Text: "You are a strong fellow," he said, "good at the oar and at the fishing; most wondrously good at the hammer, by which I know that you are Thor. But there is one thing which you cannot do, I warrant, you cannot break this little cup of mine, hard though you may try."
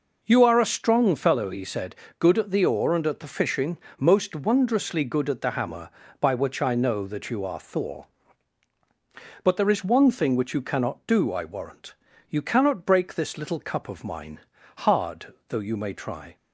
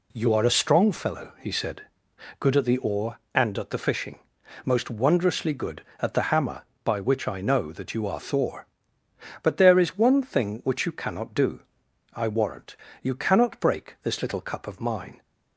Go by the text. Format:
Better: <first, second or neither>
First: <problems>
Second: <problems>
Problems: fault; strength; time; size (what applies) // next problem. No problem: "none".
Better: first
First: none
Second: stops before "hard though you may try"; at 15.2 s